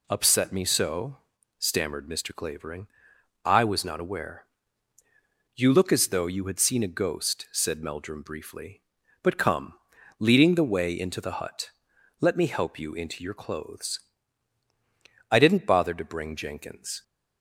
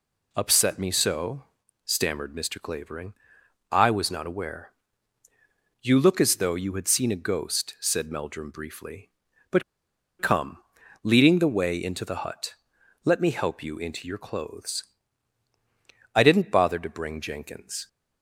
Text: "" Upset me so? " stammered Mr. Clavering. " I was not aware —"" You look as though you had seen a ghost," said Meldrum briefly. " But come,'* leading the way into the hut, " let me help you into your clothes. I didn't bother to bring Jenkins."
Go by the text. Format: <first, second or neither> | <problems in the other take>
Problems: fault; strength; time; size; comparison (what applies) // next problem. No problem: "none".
first | pauses between "But" and "come"; noticeable; at 9.6 s; 0.58 s long